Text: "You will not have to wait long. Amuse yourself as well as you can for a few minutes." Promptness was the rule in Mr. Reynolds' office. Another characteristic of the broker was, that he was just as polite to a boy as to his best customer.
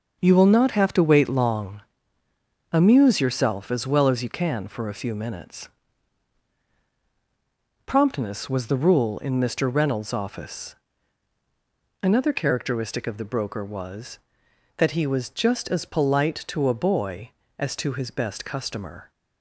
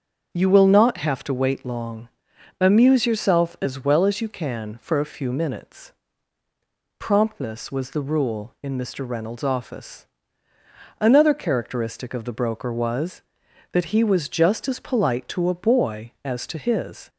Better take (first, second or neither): first